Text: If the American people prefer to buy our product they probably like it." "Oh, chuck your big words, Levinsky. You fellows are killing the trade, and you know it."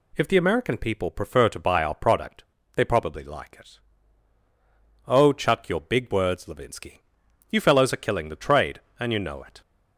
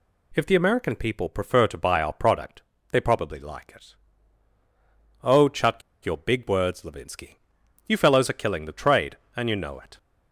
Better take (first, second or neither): first